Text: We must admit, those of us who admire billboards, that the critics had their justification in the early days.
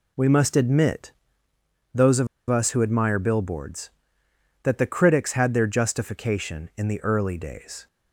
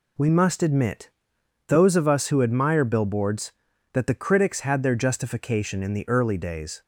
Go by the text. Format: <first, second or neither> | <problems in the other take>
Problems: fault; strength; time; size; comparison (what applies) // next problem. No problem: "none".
second | pauses between "of" and "us"; slight; at 2.2 s; 0.23 s long